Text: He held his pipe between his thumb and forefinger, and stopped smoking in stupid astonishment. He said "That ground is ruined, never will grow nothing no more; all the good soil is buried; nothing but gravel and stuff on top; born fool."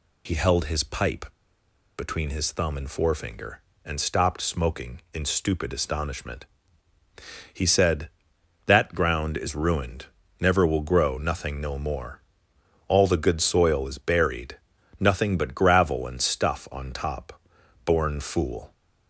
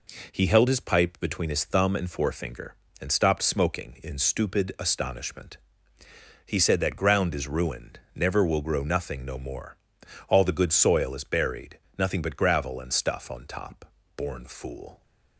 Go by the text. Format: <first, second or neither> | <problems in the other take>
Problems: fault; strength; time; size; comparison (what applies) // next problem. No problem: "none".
second | pauses between "pipe" and "between"; noticeable; at 1.2 s; 0.73 s long